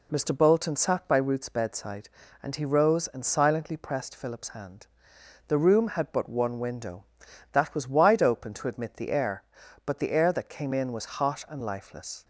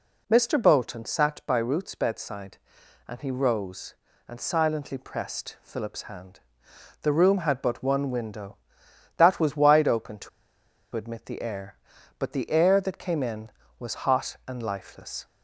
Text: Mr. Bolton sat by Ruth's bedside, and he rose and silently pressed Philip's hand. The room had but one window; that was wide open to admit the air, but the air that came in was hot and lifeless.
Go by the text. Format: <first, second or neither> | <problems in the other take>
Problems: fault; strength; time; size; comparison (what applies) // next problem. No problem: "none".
first | pauses between "to" and "admit"; noticeable; at 10.2 s; 0.65 s long